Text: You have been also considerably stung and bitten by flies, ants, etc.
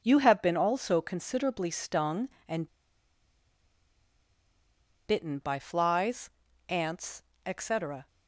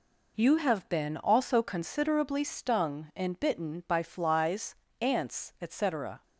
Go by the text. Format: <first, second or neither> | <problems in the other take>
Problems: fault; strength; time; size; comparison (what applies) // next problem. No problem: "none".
second | pauses between "and" and "bitten"; strong; at 2.6 s; 2.3 s long